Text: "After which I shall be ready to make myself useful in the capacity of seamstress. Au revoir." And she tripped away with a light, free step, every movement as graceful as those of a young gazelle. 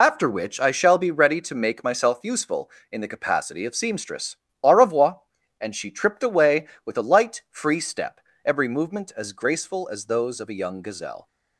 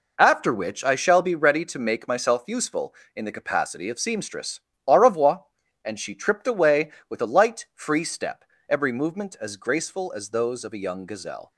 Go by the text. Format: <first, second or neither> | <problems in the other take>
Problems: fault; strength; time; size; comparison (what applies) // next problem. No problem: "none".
second | loses the start of "After"; at 0.0 s; 65 ms